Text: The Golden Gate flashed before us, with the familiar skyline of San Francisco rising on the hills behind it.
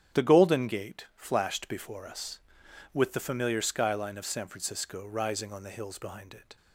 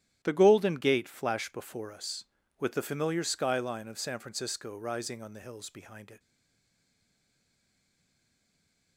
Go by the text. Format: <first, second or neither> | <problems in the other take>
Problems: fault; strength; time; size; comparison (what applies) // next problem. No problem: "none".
first | starts louder than the rest; strong; until 1.2 s; 12 dB; strong in the first // stays silent after the last word; strong; from 6.1 s on; 2.8 s long